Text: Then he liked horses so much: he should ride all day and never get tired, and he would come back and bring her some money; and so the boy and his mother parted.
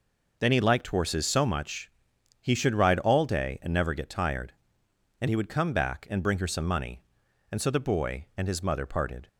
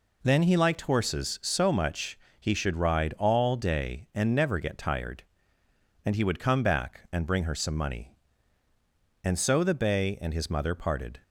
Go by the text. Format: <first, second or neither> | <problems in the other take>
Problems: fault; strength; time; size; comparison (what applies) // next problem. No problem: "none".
first | says "bay" for "boy"; at 9.7 s